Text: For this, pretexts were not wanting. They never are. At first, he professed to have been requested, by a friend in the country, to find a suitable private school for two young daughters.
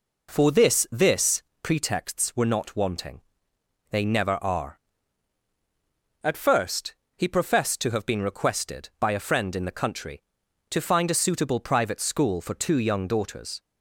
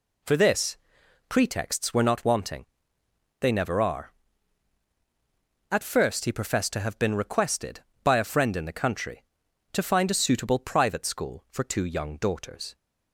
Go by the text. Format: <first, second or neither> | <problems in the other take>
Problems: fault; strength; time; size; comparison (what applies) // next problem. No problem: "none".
second | says "this" twice; at 0.9 s